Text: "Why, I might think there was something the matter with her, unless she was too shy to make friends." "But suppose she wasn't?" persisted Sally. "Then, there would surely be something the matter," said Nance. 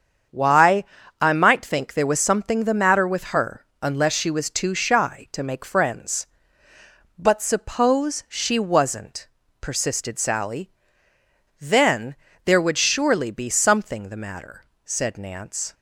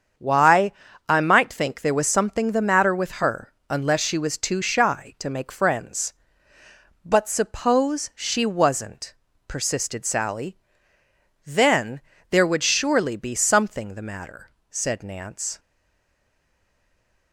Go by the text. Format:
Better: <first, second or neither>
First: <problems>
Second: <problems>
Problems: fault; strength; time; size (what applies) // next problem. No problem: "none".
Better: first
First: starts louder than the rest; strong; until 1.6 s; 7.5 dB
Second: starts louder than the rest; strong; until 1.5 s; 7.5 dB // stays silent after the last word; noticeable; from 15.5 s on; 1.8 s long